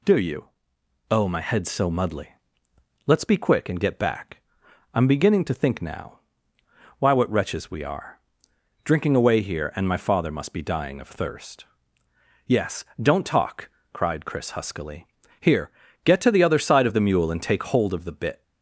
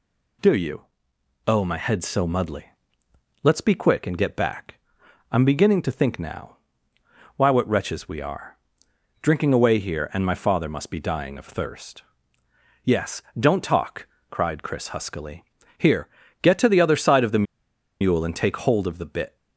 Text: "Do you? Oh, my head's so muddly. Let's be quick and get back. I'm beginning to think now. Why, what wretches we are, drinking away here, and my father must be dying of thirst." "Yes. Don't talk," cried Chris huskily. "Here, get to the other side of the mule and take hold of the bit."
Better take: first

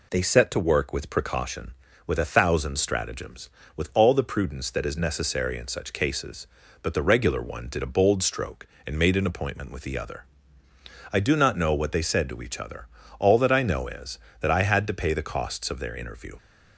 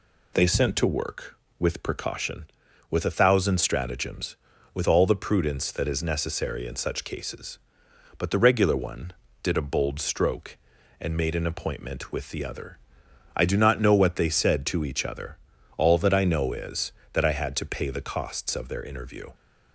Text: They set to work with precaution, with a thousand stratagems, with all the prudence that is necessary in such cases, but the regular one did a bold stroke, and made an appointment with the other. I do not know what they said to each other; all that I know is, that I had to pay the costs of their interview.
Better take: first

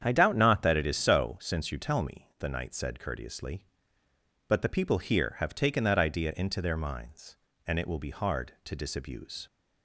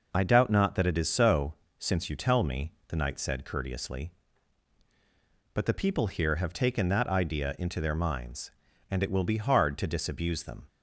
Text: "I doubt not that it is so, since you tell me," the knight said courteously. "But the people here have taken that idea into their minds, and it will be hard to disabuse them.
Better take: second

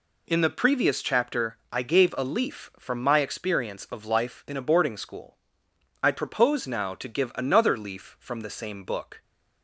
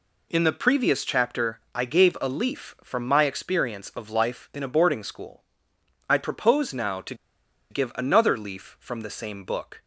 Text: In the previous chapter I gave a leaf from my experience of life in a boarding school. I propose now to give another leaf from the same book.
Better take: first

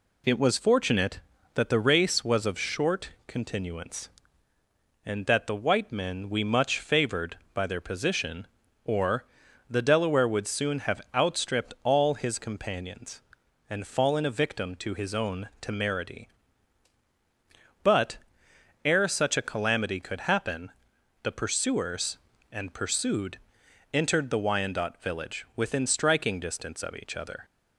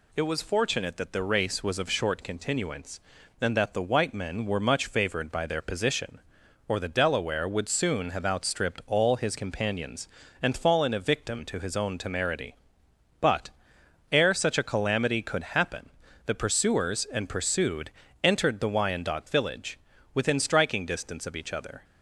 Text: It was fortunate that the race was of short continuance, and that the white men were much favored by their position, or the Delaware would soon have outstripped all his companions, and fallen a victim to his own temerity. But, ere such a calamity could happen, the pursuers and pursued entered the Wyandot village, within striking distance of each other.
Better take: second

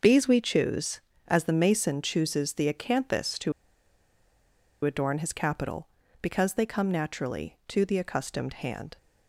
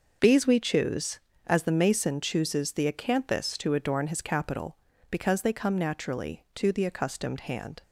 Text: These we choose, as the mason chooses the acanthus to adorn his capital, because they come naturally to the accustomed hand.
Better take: second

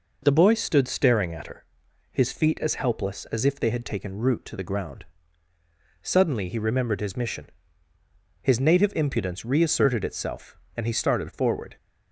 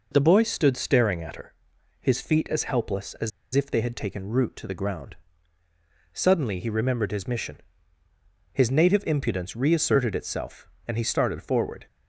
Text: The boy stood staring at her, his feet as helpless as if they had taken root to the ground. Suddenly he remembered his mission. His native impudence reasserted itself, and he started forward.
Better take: first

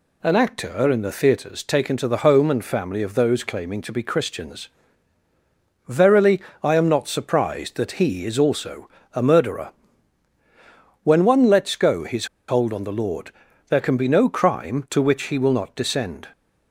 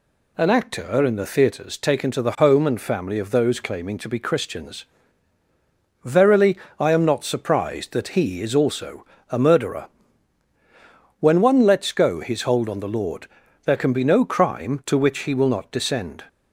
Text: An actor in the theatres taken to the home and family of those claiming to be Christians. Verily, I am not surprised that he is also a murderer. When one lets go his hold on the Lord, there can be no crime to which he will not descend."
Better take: second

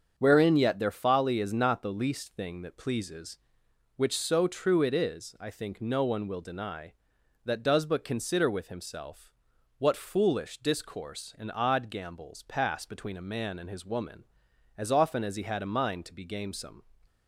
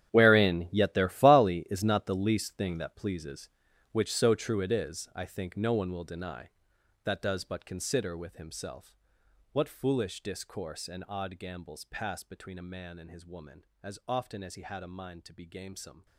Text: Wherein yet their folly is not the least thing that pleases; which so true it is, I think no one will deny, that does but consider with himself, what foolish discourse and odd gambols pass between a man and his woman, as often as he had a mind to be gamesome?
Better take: first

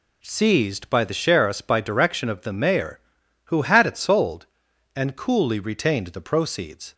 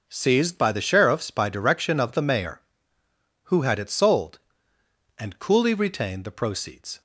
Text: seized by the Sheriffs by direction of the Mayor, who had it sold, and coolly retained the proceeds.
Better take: neither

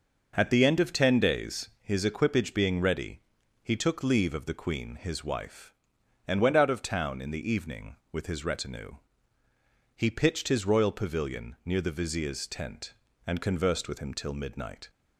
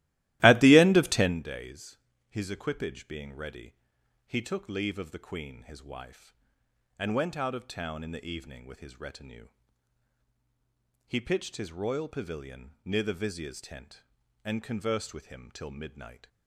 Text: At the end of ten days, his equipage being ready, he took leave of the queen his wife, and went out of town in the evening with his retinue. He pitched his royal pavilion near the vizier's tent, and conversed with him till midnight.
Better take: first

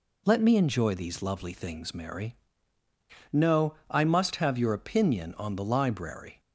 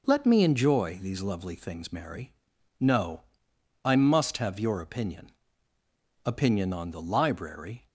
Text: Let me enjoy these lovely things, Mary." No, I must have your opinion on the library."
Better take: first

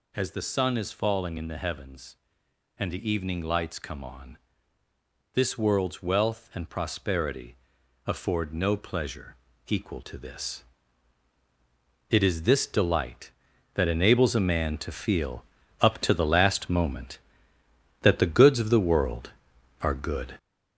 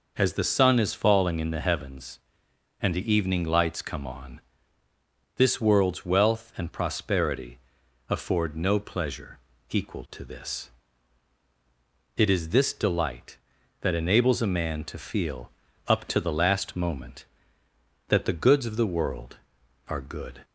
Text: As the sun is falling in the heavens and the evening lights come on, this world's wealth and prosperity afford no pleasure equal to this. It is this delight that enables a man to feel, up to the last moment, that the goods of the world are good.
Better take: second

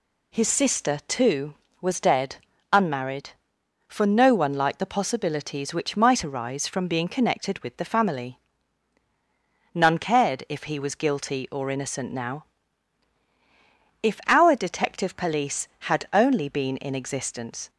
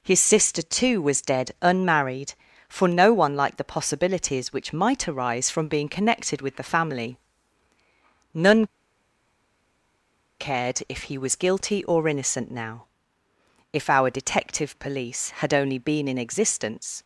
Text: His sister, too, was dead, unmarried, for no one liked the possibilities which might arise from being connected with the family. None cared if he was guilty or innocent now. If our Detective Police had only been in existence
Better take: first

